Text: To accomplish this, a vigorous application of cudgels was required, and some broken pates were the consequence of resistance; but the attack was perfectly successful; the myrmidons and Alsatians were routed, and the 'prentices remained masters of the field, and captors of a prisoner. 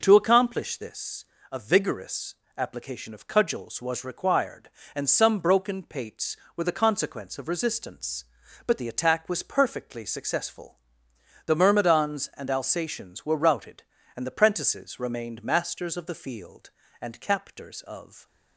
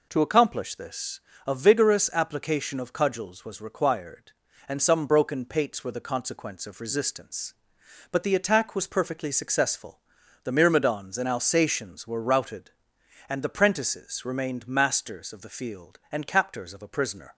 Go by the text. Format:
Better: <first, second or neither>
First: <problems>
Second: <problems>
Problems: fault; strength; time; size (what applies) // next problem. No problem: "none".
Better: second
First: pauses between "vigorous" and "application"; slight; at 2.3 s; 0.24 s long // stops before "a prisoner"; at 18.2 s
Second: none